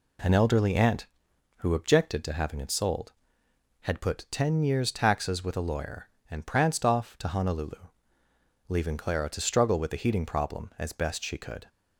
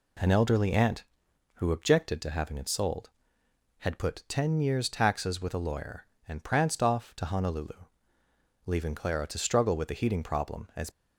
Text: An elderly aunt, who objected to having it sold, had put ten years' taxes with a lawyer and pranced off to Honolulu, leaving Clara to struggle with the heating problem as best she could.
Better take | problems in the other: first | stops before "best she could"; at 10.8 s

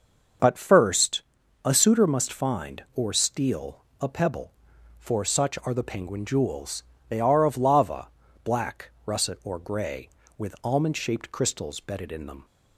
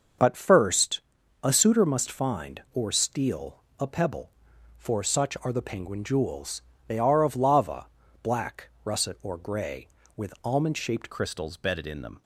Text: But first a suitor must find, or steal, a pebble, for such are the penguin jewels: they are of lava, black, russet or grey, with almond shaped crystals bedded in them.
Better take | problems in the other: first | starts louder than the rest; until 1.6 s; 6.5 dB; also in the first // pauses between "first" and "a"; at 0.9 s; 0.42 s long; also in the first // changes voice at "crystals"; from 11.1 s on; 1.1 s long

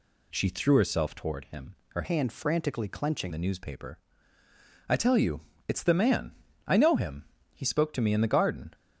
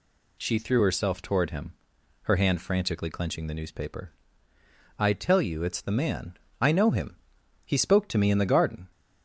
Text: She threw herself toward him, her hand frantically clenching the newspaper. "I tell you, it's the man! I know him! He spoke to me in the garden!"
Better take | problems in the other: second | changes voice from "hand" to "clenching"; from 2.0 to 3.3 s; 1.3 s long

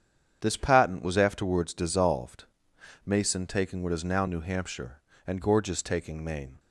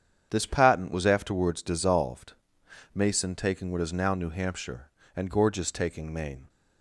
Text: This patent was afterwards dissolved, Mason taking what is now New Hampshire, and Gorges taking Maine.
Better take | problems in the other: neither | starts louder than the rest; strong; the same in both

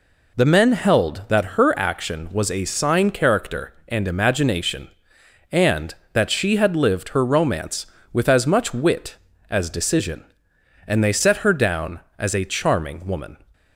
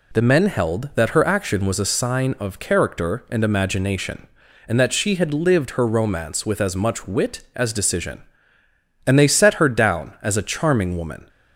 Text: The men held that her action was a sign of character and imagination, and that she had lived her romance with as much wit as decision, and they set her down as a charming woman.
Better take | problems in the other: second | skips "of"; at 3.1 s

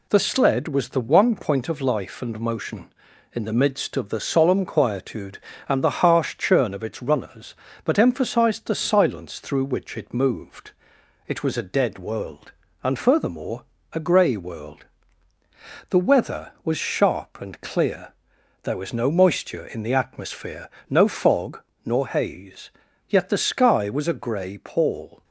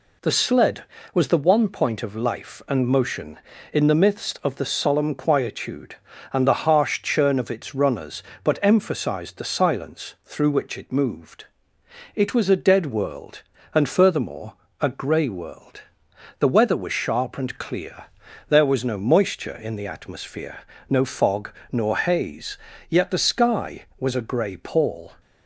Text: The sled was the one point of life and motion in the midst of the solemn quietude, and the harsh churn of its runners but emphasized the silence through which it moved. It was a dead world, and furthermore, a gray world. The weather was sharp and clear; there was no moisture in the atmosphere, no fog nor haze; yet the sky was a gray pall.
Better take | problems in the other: neither | pauses between "fog" and "nor"; slight; the same in both

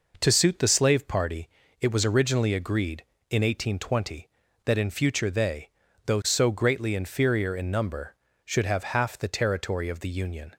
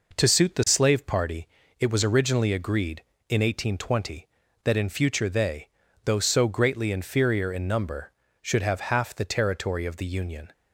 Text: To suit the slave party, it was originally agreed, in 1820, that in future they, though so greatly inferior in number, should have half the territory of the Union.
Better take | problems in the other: neither | none

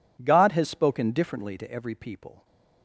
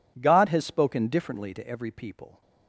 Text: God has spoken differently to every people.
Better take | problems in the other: neither | none

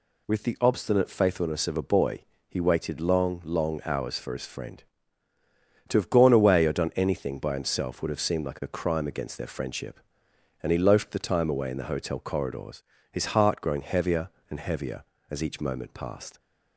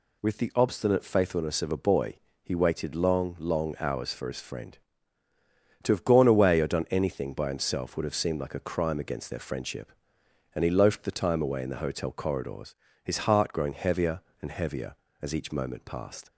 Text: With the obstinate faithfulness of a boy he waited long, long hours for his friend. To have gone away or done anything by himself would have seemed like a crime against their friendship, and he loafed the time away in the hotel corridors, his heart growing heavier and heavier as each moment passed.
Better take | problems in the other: neither | pauses between "boy" and "he"; slight; the same in both

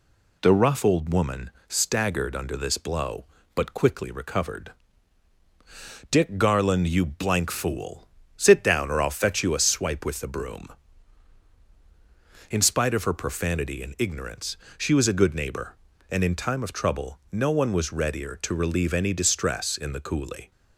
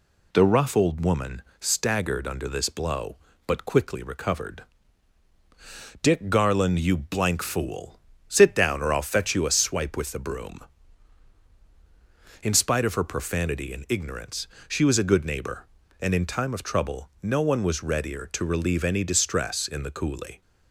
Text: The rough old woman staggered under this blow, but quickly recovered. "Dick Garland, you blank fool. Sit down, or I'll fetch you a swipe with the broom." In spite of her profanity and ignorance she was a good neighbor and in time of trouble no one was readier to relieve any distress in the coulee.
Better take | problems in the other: neither | pauses between "woman" and "staggered"; slight; the same in both // pauses between "ignorance" and "she"; slight; the same in both

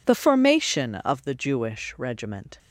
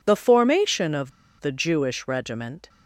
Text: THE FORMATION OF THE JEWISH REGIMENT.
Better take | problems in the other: first | pauses between "OF" and "THE"; slight; at 1.1 s; 0.29 s long

